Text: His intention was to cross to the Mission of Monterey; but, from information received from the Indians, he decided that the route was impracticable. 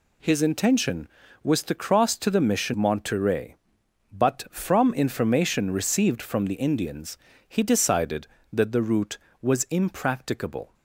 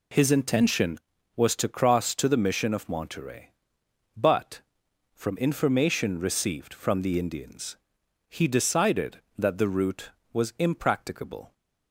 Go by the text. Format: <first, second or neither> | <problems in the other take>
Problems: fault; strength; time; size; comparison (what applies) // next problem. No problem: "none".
second | skips "of"; at 2.7 s